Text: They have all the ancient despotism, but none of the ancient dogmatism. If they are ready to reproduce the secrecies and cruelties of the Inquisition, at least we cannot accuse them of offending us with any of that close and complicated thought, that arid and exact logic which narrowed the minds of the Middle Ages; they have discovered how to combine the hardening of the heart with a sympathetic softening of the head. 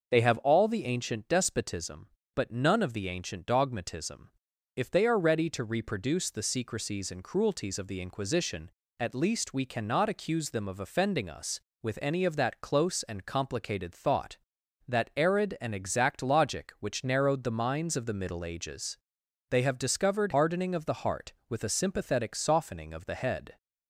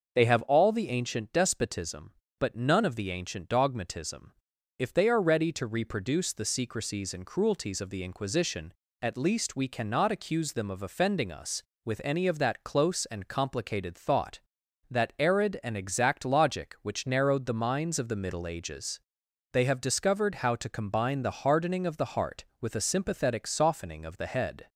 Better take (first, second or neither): second